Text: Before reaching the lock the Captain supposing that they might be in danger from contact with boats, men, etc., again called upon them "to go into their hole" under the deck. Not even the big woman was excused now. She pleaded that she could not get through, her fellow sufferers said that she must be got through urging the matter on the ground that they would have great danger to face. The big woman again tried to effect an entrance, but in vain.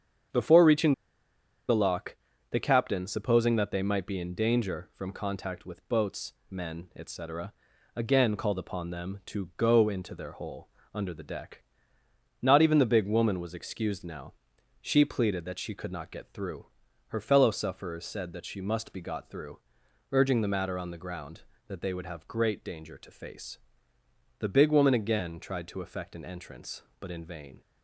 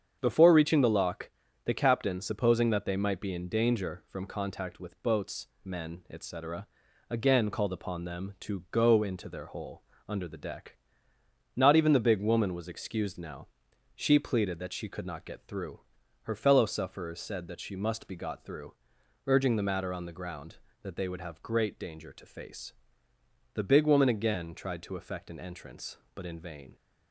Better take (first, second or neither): second